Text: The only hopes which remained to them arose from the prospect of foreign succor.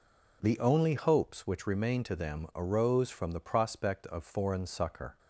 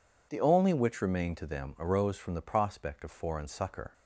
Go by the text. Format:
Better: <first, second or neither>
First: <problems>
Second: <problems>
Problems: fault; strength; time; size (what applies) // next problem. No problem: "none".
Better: first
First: none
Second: skips "hopes"; at 0.7 s